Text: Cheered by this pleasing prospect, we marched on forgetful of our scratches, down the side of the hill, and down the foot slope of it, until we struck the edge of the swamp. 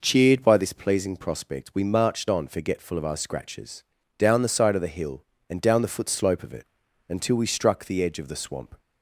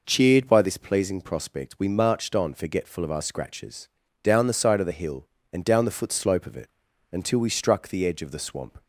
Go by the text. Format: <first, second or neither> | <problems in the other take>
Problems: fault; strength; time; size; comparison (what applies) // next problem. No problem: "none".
neither | none